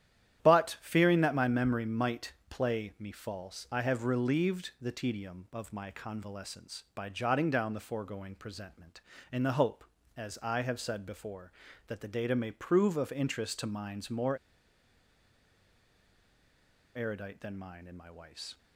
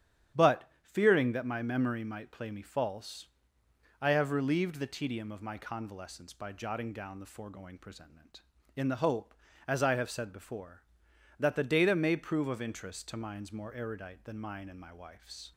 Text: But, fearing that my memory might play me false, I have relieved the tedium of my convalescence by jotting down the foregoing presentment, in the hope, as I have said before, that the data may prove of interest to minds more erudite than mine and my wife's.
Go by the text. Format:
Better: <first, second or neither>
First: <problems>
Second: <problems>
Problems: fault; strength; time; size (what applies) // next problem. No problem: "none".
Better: second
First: starts louder than the rest; strong; until 1.4 s; 11 dB // pauses between "might" and "play"; slight; at 2.3 s; 0.16 s long // pauses between "more" and "erudite"; strong; at 14.3 s; 2.5 s long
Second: starts louder than the rest; strong; until 1.5 s; 9.5 dB